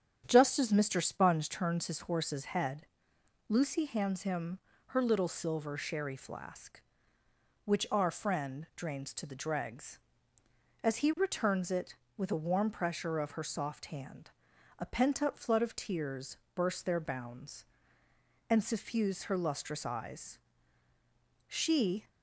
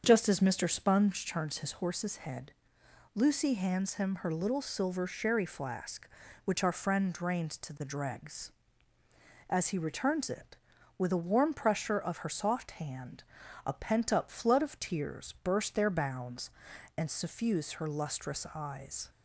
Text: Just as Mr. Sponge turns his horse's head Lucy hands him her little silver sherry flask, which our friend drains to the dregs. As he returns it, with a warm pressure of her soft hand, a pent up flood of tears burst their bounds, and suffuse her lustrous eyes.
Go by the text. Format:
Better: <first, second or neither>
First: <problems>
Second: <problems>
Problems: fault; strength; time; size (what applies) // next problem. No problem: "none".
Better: second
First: starts louder than the rest; strong; until 1.2 s; 8.5 dB // pauses between "head" and "Lucy"; noticeable; at 2.8 s; 0.62 s long // pauses between "him" and "her"; slight; at 4.5 s; 0.28 s long // pauses between "tears" and "burst"; slight; at 16.3 s; 0.18 s long // goes on to say "She"; noticeable; from 21.4 s on; 0.62 s long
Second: starts louder than the rest; until 1.0 s; 7 dB // pauses between "head" and "Lucy"; noticeable; at 2.5 s; 0.64 s long